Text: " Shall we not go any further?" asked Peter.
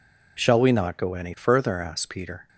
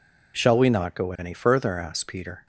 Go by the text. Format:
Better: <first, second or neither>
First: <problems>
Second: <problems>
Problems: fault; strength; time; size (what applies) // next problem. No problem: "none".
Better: neither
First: none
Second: none